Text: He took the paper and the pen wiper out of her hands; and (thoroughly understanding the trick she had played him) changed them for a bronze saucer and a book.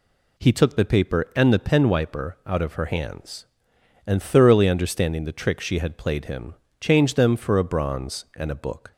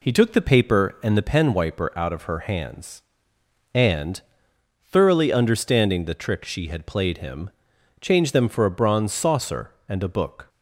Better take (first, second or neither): second